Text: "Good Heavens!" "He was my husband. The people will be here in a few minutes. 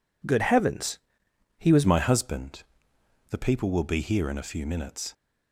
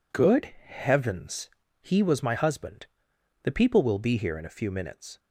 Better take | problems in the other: second | changes voice at "my"; from 1.8 s on; 3.3 s long

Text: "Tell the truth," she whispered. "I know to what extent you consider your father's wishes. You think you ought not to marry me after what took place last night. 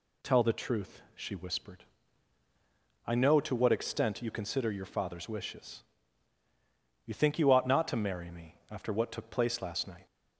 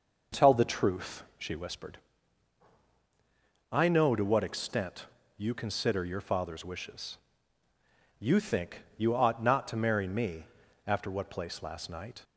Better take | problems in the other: first | pauses between "extent" and "you"; slight; at 5.0 s; 0.32 s long // pauses between "think" and "you"; slight; at 8.8 s; 0.16 s long // pauses between "me" and "after"; at 10.4 s; 0.40 s long // skips "took"; at 11.2 s

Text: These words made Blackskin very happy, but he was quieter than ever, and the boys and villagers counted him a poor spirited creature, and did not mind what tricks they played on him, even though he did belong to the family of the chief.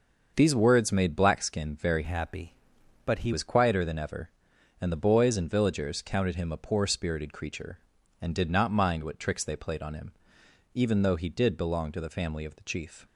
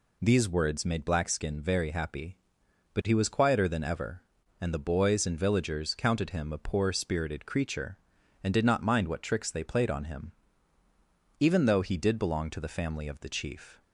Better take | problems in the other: second | starts louder than the rest; until 1.3 s; 6.5 dB // changes voice from "happy" to "he"; from 2.0 to 3.3 s; 1.3 s long

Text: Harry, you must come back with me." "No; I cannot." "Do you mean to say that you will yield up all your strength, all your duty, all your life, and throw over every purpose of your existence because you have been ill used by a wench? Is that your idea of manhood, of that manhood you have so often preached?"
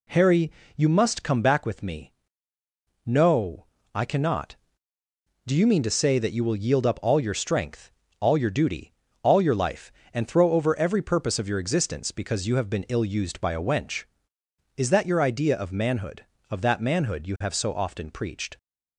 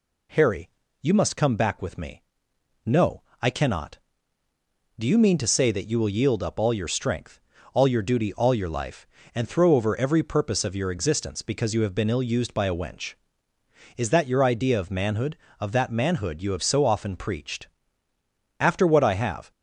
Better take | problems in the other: first | goes on to say "After what I have"; noticeable; from 18.5 s on; 0.92 s long

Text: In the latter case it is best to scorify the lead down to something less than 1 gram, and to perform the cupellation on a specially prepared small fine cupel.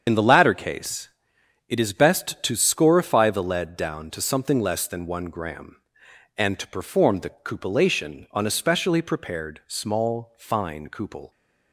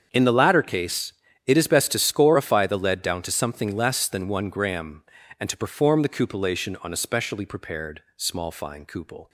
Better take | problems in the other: second | loses the start of "In"; at 0.0 s; 45 ms // starts louder than the rest; strong; until 1.0 s; 7.5 dB; strong in the second // pauses between "case" and "it"; noticeable; at 1.0 s; 0.60 s long; slight in the second

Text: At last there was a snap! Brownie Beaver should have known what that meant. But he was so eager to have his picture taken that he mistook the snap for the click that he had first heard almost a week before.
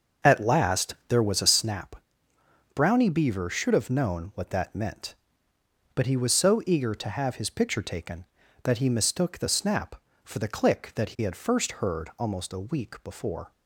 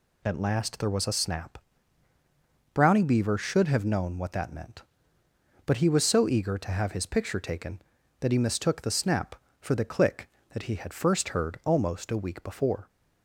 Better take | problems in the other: second | starts louder than the rest; noticeable; until 1.6 s; 6 dB

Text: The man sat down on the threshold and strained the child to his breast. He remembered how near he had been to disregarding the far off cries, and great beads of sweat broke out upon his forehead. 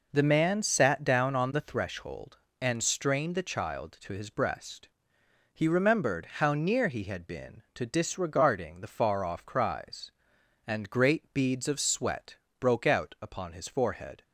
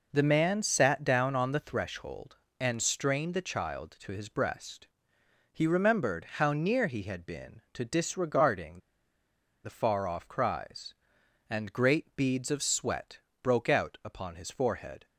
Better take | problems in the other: first | pauses between "disregarding" and "the"; noticeable; at 8.7 s; 0.84 s long // pauses between "sweat" and "broke"; slight; at 13.1 s; 0.24 s long; slight in the first

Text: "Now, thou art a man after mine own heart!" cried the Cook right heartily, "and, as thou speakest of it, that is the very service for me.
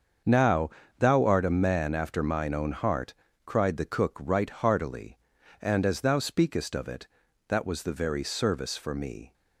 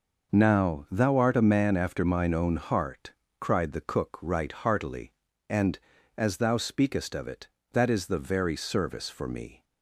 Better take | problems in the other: second | starts louder than the rest; until 1.5 s; 6.5 dB // says "was" for "is"; at 7.6 s

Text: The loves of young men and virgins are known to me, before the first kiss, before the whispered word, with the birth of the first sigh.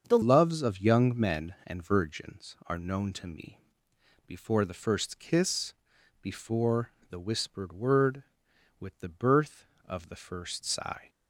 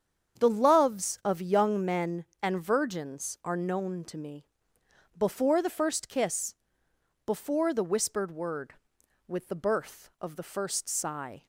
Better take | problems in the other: second | starts louder than the rest; until 1.1 s; 7 dB; strong in the second // changes voice at "loves"; from 0.2 s on; 10.8 s long // pauses between "before" and "the"; slight; at 6.9 s; 0.18 s long

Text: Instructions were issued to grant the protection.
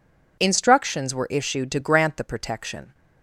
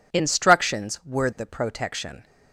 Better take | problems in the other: first | skips "issued to grant"; at 1.3 s

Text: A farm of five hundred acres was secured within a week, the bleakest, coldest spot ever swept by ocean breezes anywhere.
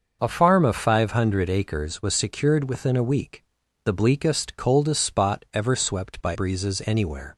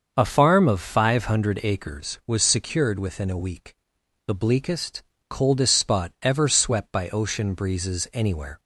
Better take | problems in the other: second | starts louder than the rest; until 1.2 s; 6 dB; also in the second // skips "ocean"; at 6.3 s

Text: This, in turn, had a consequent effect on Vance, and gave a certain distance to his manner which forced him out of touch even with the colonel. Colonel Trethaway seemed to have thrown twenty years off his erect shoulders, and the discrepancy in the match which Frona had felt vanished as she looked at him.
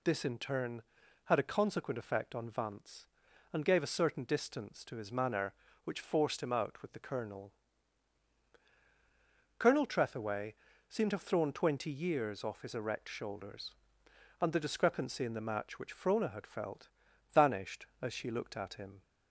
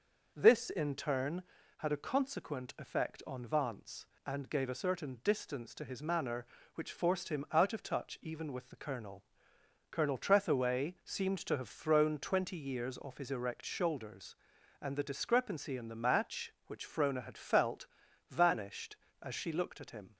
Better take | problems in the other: second | skips "of touch even"; at 6.8 s // pauses between "Trethaway" and "seemed"; slight; at 10.5 s; 0.34 s long // pauses between "felt" and "vanished"; at 16.8 s; 0.44 s long; also in the second

